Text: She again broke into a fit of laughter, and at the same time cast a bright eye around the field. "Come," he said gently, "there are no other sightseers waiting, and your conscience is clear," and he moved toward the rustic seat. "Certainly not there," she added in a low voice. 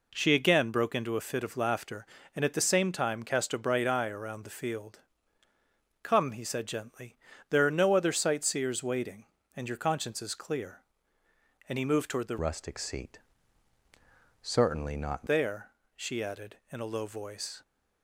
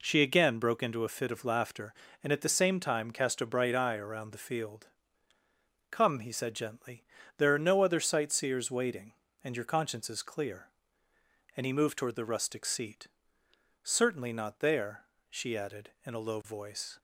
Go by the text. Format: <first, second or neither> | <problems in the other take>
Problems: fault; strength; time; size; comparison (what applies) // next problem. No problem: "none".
second | changes voice from "rustic" to "not"; from 12.4 to 15.2 s; 2.8 s long